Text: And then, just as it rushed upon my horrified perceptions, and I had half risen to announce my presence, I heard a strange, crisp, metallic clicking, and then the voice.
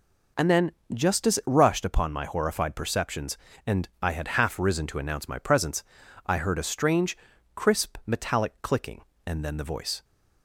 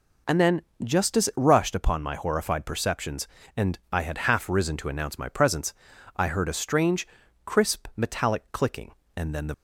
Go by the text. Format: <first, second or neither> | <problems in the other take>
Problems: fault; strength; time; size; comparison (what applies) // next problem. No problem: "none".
first | stops before "voice"; at 9.5 s